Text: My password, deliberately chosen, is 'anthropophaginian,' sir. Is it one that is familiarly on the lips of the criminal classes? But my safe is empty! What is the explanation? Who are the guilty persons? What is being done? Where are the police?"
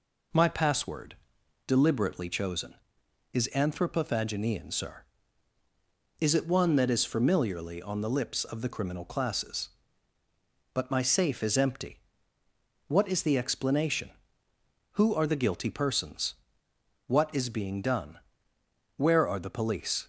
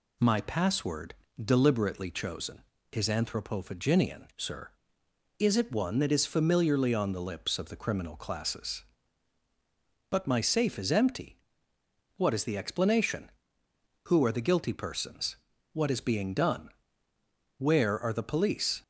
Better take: neither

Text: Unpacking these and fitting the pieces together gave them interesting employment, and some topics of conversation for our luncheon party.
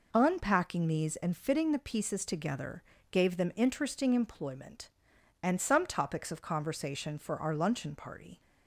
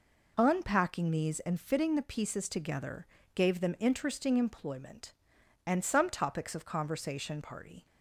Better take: first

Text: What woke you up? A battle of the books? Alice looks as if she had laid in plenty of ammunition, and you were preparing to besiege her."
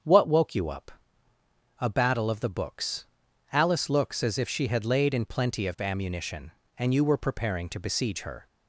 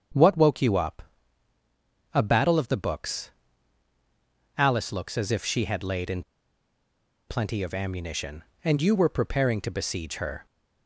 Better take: first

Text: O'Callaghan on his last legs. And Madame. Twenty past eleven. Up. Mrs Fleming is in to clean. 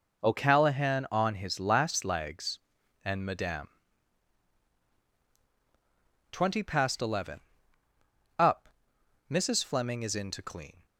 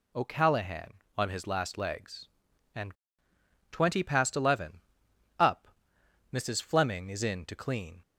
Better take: first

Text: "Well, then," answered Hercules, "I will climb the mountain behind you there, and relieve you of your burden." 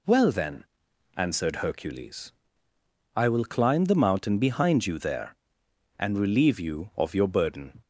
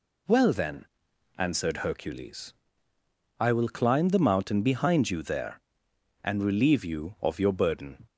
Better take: neither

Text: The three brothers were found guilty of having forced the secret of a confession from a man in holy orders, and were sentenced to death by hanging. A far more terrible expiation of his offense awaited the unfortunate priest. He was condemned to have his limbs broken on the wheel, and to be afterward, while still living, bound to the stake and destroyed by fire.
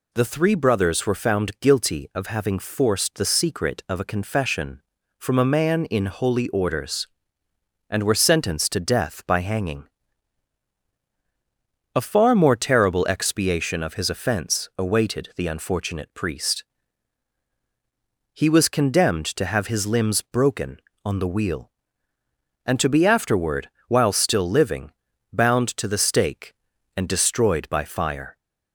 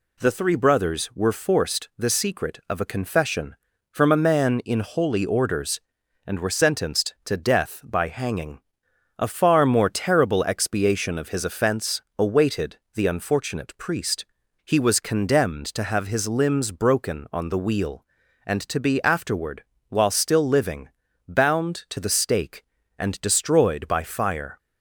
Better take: first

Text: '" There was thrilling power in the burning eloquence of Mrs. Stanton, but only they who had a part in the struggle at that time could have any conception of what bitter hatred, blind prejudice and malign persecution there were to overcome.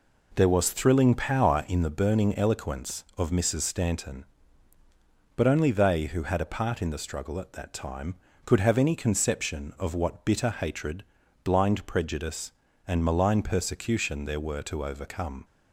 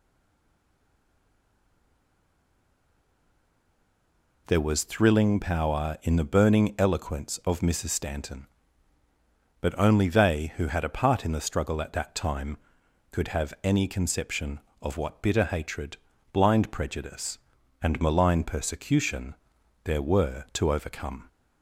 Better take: first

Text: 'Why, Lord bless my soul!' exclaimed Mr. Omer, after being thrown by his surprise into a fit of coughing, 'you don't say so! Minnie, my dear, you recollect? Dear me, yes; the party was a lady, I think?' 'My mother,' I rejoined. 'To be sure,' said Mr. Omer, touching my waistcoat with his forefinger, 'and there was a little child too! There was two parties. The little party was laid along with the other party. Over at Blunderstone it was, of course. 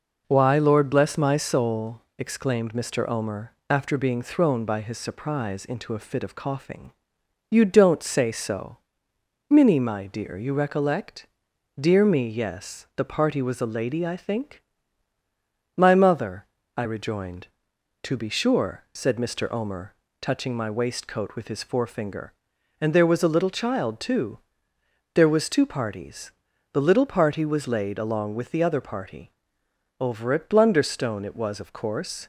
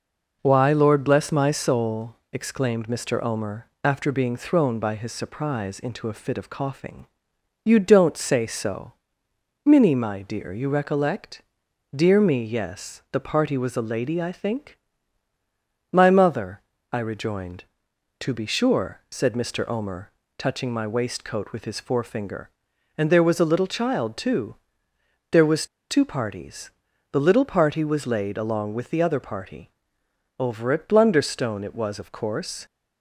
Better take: first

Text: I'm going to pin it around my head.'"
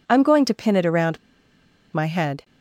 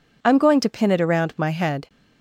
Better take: second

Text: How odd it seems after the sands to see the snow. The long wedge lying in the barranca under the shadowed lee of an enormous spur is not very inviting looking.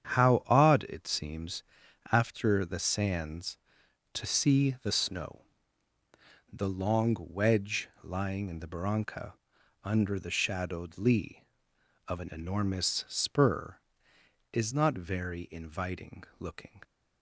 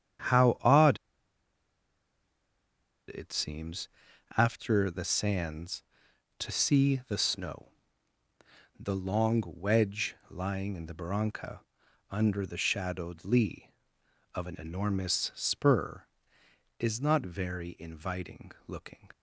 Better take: first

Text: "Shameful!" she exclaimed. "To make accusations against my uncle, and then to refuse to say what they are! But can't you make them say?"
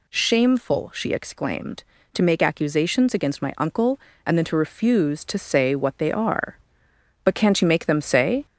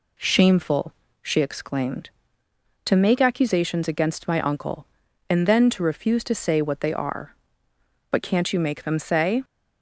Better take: second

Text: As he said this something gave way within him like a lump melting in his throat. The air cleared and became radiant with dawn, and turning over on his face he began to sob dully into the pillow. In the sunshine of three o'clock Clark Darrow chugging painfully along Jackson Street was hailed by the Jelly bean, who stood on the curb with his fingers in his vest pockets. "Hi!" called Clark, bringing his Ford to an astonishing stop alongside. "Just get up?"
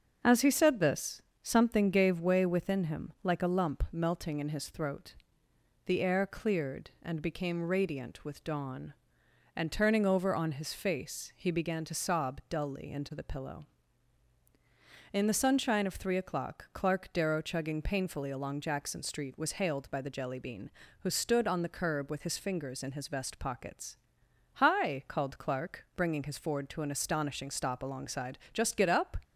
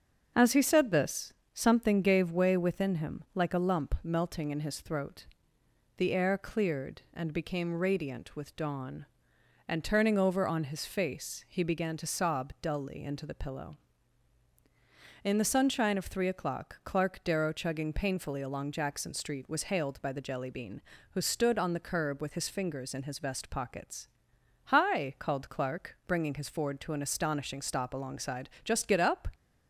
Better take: neither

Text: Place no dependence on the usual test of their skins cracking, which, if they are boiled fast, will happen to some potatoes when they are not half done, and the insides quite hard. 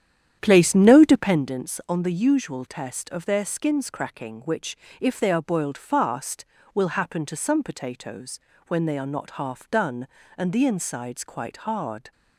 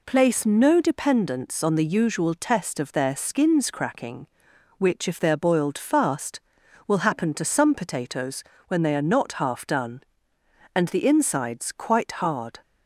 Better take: second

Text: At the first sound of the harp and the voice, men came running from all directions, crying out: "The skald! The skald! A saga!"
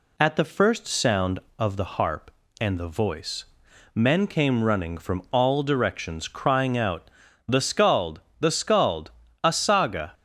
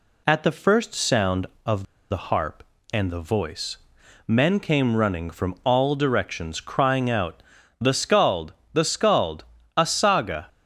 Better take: first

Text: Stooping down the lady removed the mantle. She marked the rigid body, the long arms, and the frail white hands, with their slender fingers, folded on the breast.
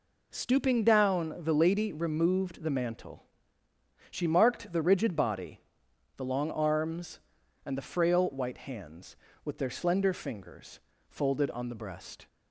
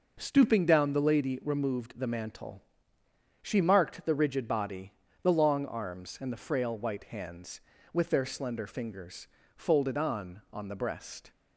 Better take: first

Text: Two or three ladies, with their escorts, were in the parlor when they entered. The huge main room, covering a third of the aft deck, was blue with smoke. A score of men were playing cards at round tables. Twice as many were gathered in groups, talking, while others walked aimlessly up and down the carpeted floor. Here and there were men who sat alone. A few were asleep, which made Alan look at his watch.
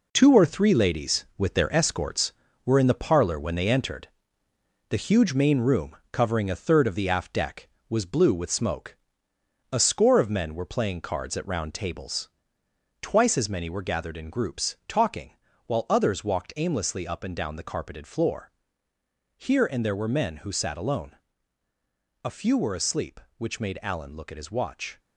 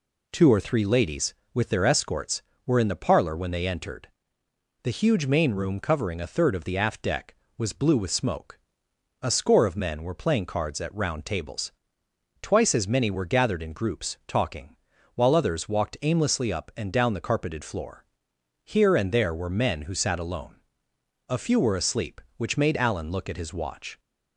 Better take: second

